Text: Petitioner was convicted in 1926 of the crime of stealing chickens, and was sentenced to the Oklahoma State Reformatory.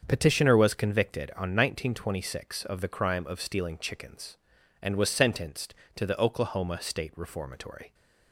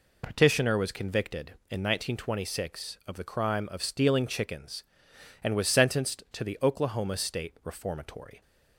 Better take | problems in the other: second | starts louder than the rest; until 1.0 s; 7 dB // says "on" for "in"; at 1.3 s

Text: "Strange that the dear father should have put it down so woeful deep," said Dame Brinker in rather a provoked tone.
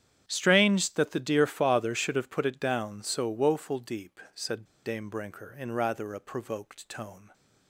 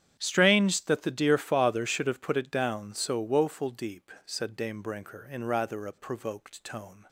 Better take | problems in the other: second | starts louder than the rest; strong; until 1.2 s; 9.5 dB; strong in the second // pauses between "said" and "Dame"; slight; at 4.6 s; 0.21 s long

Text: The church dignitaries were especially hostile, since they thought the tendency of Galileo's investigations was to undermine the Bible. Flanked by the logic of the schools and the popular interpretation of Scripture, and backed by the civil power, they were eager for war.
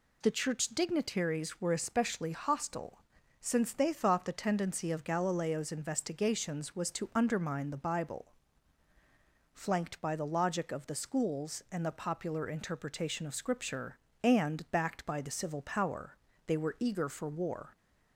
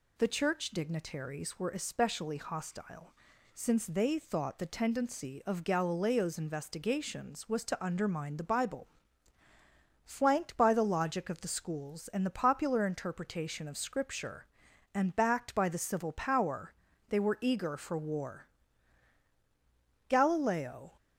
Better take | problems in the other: first | goes on to say "Galileo"; noticeable; from 20.0 s on; 0.88 s long

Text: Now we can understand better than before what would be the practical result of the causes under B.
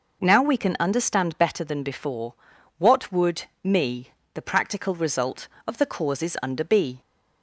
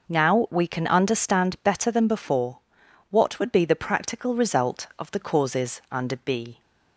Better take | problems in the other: second | pauses between "before" and "what"; at 2.3 s; 0.42 s long; noticeable in the second // says "me" for "be"; at 3.6 s

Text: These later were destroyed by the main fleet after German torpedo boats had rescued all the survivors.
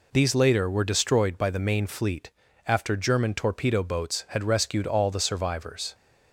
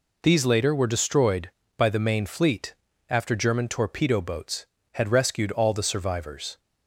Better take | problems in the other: neither | pauses between "fleet" and "after"; slight; the same in both

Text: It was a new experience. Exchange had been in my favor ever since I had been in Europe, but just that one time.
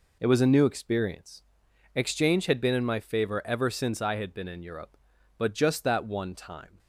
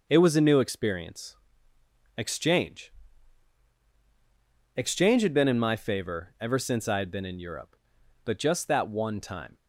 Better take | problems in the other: first | says "Exchange" twice; at 4.7 s

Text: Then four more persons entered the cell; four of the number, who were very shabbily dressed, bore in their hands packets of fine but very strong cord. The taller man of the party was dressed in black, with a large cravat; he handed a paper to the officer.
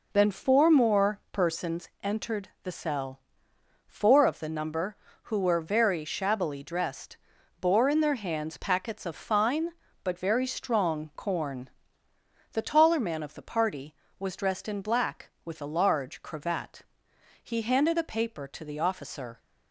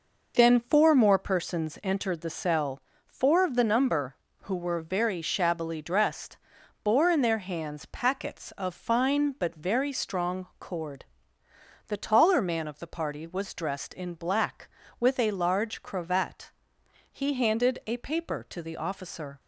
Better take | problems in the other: second | pauses between "persons" and "entered"; slight; at 1.8 s; 0.16 s long // says "corn" for "cord"; at 11.1 s

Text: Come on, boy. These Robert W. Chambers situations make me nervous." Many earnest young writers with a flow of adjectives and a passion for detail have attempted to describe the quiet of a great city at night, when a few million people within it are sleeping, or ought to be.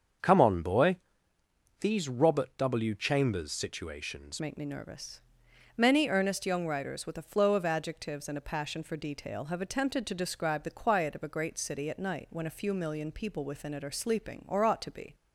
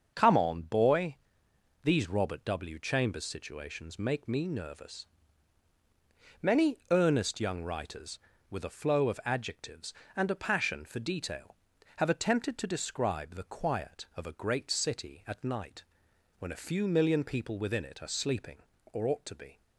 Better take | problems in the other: second | starts louder than the rest; until 2.0 s; 7 dB; also in the second // changes voice at "make"; from 4.4 s on; 10.7 s long

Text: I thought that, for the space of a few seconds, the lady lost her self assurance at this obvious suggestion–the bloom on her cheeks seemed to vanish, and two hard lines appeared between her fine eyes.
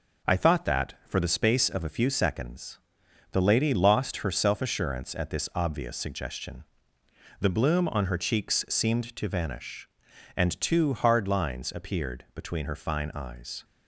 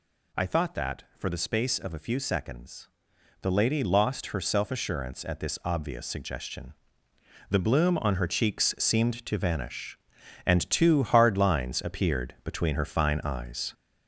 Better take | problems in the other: first | gets louder; noticeable; throughout; 4.5 dB

